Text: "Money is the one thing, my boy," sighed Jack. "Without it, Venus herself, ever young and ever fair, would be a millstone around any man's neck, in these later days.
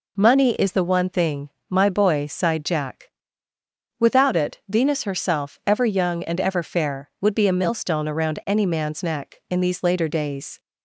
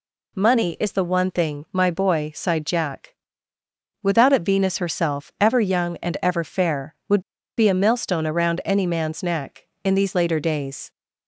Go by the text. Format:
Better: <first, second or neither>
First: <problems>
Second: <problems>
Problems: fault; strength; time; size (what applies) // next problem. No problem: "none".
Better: first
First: none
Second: pauses between "would" and "be"; at 7.2 s; 0.36 s long